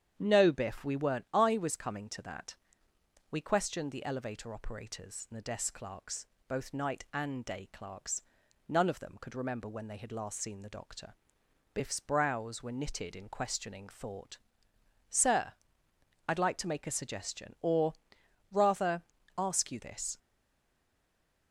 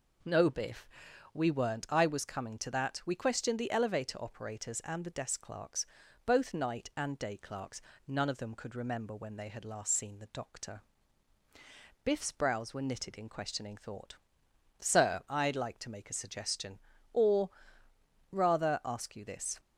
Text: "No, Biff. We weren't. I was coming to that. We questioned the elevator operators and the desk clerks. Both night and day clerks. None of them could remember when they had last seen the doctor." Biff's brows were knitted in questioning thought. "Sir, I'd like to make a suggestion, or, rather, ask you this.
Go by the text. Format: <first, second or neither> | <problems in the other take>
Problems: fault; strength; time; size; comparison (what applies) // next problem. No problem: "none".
second | starts louder than the rest; strong; until 1.1 s; 8.5 dB // stays silent after the last word; noticeable; from 20.1 s on; 1.4 s long